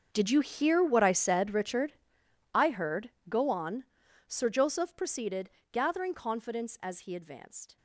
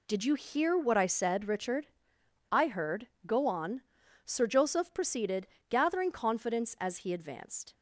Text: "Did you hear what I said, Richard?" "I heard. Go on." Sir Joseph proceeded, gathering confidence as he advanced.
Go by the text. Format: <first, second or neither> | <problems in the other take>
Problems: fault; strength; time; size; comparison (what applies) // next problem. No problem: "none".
second | gets quieter; strong; throughout; 18.5 dB